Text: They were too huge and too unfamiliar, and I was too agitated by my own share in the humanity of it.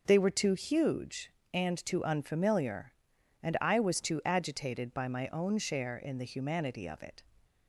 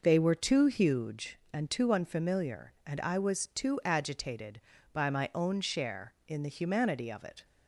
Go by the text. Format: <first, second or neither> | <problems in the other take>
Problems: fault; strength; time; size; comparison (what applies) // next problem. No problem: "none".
neither | none